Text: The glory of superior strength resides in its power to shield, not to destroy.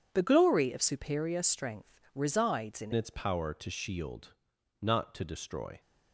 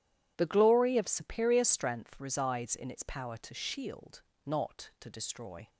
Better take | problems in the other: second | pauses between "strength" and "resides"; slight; at 2.0 s; 0.16 s long // changes voice at "its"; from 2.9 s on; 2.8 s long

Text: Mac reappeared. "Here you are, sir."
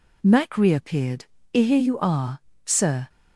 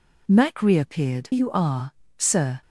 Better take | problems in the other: first | skips "Here"; at 1.3 s

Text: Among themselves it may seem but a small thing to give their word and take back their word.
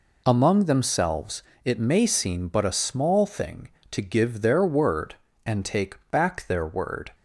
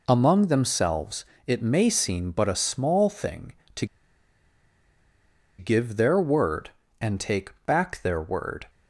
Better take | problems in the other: first | pauses between "themselves" and "it"; slight; at 1.2 s; 0.22 s long; slight in the first // pauses between "to" and "give"; strong; at 3.8 s; 1.7 s long

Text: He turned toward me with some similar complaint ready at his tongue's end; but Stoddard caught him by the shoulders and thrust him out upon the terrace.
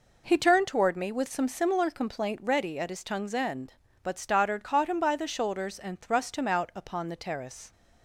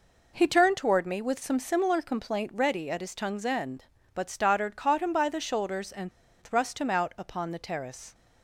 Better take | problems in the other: first | pauses between "and" and "thrust"; slight; at 6.1 s; 0.30 s long

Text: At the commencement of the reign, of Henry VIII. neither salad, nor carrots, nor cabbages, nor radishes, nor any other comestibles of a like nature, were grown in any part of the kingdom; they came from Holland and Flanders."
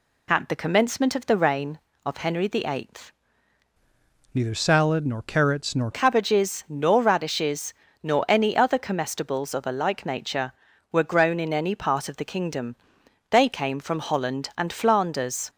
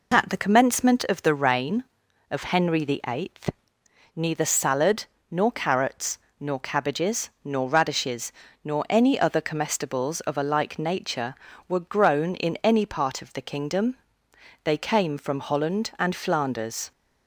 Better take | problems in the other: second | changes voice from "neither" to "nor"; from 4.3 to 5.8 s; 1.5 s long

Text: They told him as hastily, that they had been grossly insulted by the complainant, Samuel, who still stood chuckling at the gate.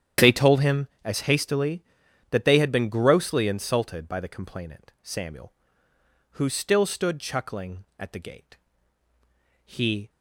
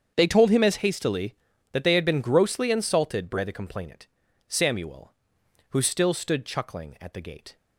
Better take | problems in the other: second | starts louder than the rest; strong; until 1.4 s; 10 dB; strong in the second // goes on to say "He"; slight; from 9.6 s on; 0.44 s long

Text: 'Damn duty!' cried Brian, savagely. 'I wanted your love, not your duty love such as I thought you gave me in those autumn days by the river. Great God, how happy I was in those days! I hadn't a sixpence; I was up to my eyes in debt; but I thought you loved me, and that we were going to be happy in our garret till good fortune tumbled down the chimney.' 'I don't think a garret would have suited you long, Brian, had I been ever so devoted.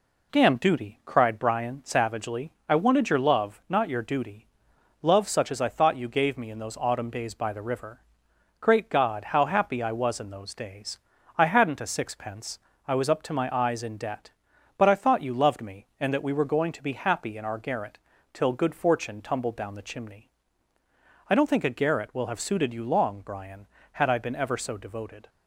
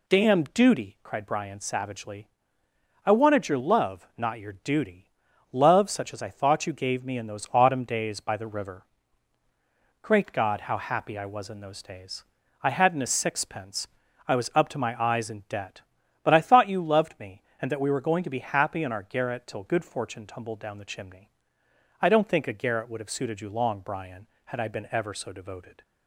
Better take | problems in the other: second | pauses between "duty" and "love"; noticeable; at 4.4 s; 0.56 s long; noticeable in the second // pauses between "garret" and "till"; slight; at 17.9 s; 0.36 s long // says "will" for "would"; at 22.1 s

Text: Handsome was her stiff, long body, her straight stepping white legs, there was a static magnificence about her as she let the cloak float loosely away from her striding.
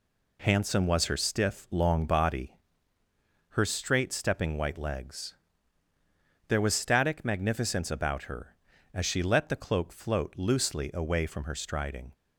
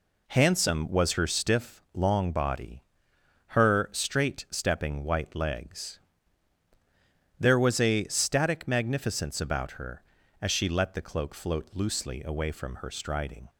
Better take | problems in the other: second | skips "a"; at 6.7 s

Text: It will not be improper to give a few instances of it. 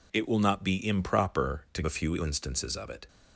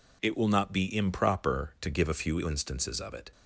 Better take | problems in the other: second | skips "give"; at 1.8 s

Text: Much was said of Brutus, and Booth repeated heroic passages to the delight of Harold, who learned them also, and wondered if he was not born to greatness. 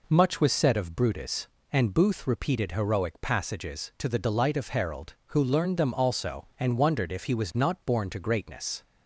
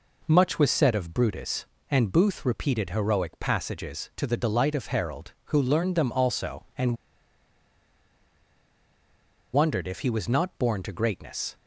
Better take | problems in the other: first | pauses between "and" and "wondered"; strong; at 6.9 s; 2.5 s long

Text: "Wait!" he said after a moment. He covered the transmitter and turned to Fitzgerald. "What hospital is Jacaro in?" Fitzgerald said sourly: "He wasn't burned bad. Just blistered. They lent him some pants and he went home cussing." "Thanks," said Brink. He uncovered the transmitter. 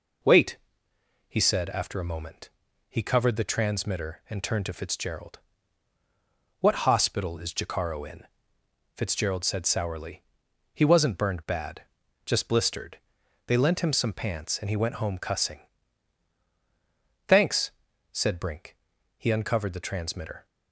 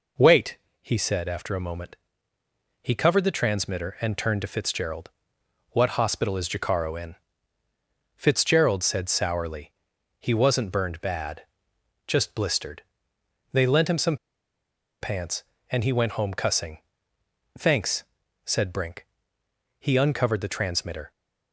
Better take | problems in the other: first | pauses between "some" and "pants"; noticeable; at 14.1 s; 0.85 s long

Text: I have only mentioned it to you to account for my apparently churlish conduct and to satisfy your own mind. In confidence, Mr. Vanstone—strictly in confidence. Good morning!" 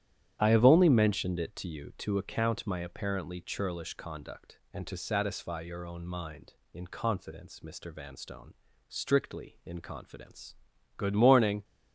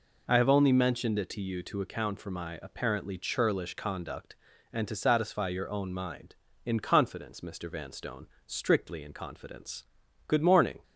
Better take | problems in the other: second | starts louder than the rest; strong; until 1.4 s; 10 dB // skips "for"; at 2.6 s

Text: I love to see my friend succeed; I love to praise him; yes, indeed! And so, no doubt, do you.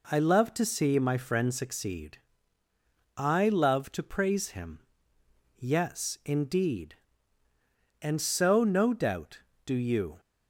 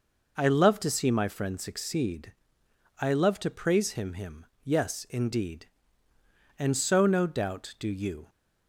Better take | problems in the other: first | says "him" twice; at 4.1 s

